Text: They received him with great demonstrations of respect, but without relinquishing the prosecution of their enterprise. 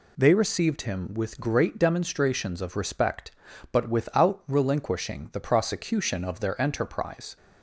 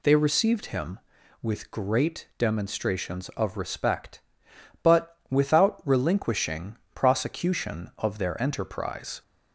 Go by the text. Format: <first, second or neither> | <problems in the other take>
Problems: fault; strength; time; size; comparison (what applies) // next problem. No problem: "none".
first | skips "the"; at 6.8 s